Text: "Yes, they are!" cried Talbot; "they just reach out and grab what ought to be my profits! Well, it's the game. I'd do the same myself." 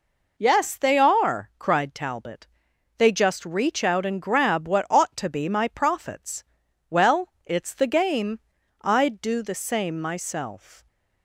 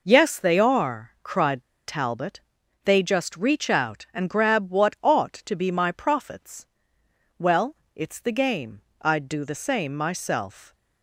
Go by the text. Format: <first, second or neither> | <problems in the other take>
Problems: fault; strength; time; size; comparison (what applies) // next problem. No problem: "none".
first | pauses between "cried" and "Talbot"; slight; at 1.6 s; 0.23 s long